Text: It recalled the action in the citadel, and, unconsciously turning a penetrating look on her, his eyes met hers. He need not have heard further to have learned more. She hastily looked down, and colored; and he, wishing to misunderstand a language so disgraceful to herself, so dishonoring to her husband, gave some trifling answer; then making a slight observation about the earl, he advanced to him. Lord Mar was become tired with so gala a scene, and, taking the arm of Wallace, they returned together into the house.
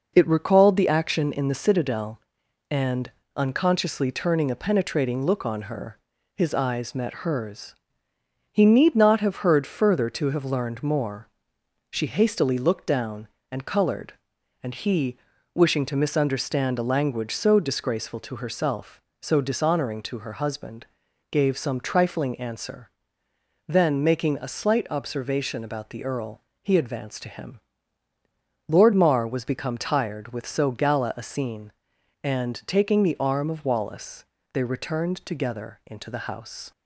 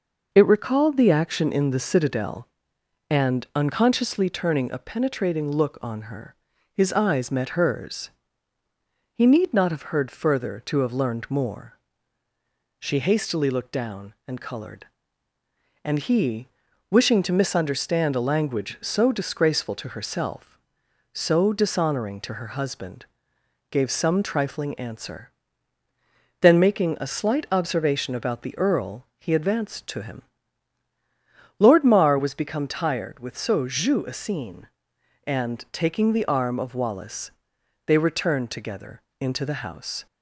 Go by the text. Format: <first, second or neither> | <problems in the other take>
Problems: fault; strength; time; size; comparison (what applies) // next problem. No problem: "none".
first | says "jeu" for "gala"; at 33.6 s // pauses between "together" and "into"; slight; at 39.0 s; 0.18 s long